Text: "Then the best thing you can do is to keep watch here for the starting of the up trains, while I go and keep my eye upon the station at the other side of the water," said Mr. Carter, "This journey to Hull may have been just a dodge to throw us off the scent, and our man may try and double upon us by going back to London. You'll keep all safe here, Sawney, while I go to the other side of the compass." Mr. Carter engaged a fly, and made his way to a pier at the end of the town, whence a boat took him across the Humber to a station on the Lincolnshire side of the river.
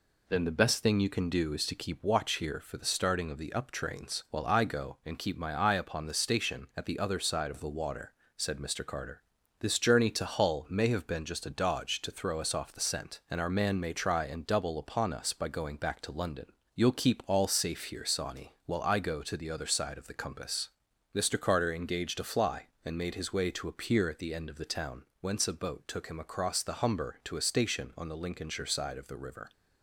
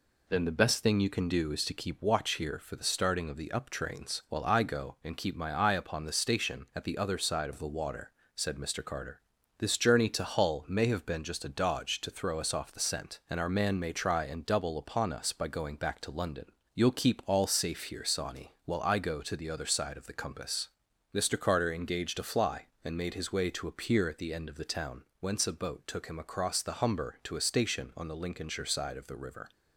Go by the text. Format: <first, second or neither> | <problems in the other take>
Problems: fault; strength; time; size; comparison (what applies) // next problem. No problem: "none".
neither | none